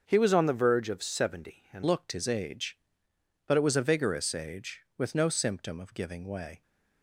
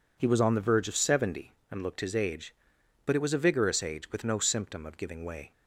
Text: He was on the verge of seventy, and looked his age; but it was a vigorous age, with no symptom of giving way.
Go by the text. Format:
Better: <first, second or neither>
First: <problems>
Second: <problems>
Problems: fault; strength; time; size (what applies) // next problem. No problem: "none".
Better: second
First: starts louder than the rest; until 1.0 s; 6.5 dB // changes voice at "looked"; from 1.8 s on; 4.8 s long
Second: none